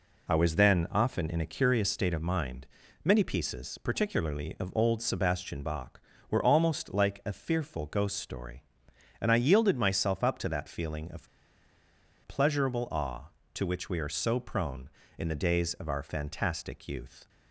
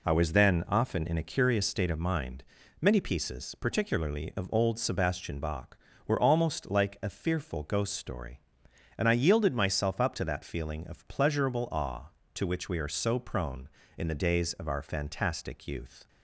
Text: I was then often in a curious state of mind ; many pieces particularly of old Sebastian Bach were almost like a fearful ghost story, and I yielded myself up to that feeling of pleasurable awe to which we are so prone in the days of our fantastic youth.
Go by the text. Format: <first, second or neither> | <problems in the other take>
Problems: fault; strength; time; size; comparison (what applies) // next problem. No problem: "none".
second | pauses between "of" and "pleasurable"; noticeable; at 11.2 s; 0.98 s long